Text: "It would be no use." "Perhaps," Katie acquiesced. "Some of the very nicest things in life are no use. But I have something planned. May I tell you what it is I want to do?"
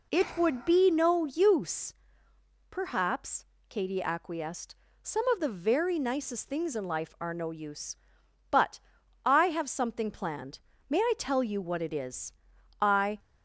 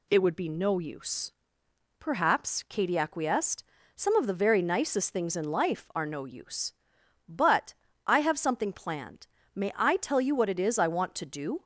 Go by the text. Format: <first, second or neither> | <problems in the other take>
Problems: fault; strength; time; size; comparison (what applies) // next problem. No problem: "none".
second | pauses between "But" and "I"; noticeable; at 8.7 s; 0.46 s long; slight in the second // pauses between "is" and "I"; noticeable; at 12.3 s; 0.50 s long // stops before "want to do"; at 13.1 s